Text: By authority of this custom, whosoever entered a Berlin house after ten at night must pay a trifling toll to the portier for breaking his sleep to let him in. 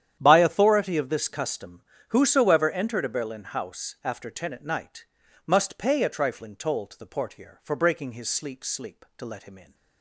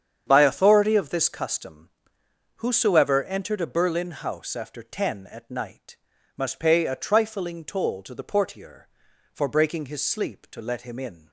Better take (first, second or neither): second